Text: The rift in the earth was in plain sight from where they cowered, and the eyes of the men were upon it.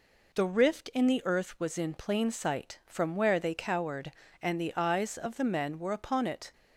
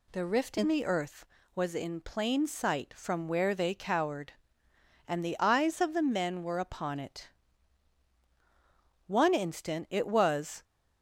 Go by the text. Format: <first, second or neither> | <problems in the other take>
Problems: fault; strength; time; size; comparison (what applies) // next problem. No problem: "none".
first | goes on to say "One instant it was"; from 9.0 s on; 1.5 s long